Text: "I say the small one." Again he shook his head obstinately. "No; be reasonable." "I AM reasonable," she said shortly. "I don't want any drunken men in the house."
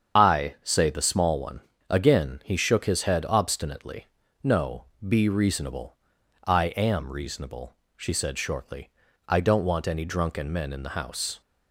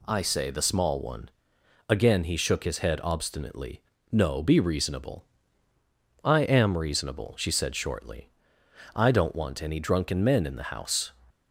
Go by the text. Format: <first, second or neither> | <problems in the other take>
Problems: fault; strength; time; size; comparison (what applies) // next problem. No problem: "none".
second | loses the start of "I"; at 0.1 s; 50 ms // starts louder than the rest; strong; until 1.2 s; 7.5 dB